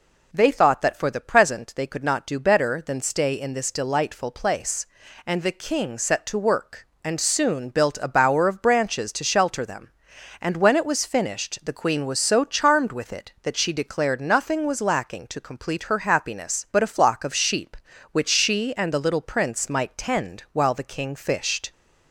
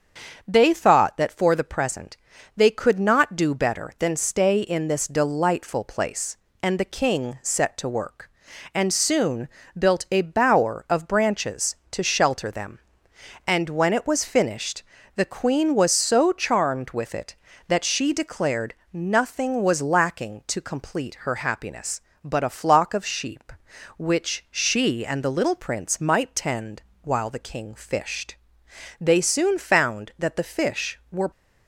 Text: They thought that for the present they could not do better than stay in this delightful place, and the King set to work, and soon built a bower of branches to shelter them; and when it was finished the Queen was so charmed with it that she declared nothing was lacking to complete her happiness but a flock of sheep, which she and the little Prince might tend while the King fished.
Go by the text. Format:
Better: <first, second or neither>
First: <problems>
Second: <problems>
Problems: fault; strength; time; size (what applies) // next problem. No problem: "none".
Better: first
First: none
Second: starts louder than the rest; until 1.4 s; 6.5 dB // pauses between "present" and "they"; at 2.1 s; 0.38 s long // pauses between "soon" and "built"; slight; at 9.4 s; 0.28 s long // pauses between "finished" and "the"; slight; at 14.8 s; 0.32 s long // pauses between "declared" and "nothing"; slight; at 18.7 s; 0.18 s long // pauses between "tend" and "while"; slight; at 26.8 s; 0.20 s long // goes on to say "They soon found that the fish were"; strong; from 28.9 s on; 2.3 s long